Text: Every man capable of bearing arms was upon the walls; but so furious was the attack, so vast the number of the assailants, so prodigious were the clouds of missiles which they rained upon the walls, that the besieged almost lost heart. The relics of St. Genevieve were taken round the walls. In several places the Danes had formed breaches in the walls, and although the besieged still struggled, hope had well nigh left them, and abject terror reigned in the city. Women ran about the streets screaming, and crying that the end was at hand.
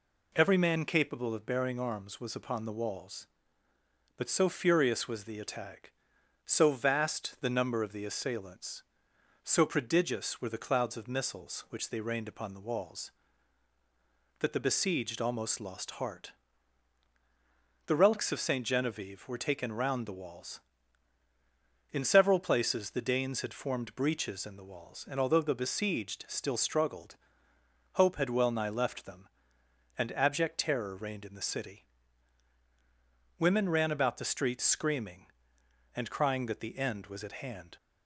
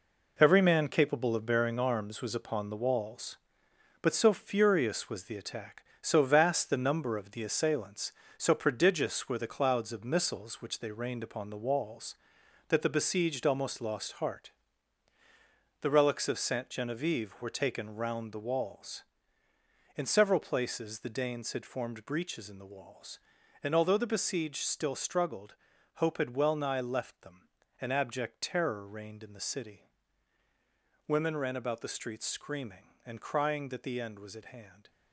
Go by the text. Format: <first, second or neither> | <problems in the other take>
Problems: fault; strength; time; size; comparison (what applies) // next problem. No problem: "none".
first | gets quieter; strong; throughout; 8 dB